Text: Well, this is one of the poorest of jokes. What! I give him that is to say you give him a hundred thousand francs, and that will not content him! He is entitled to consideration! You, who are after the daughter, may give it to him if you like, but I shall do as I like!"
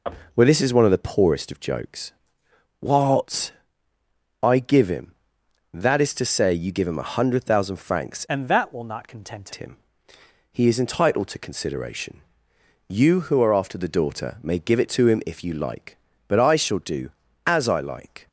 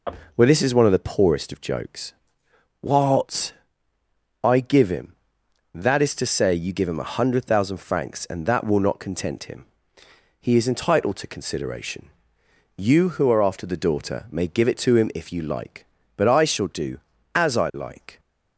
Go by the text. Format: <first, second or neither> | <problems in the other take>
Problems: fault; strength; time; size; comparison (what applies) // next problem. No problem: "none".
second | changes voice from "and" to "content"; from 8.2 to 9.4 s; 1.2 s long